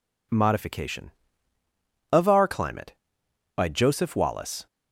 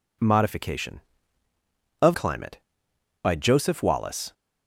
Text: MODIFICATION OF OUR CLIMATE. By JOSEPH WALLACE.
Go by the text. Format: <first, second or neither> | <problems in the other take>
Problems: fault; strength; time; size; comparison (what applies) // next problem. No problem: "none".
first | skips "OUR"; at 2.1 s